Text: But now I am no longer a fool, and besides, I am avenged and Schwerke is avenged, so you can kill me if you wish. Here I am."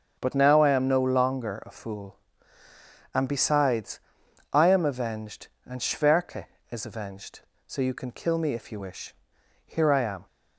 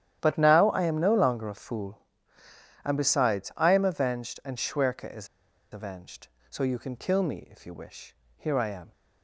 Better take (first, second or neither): first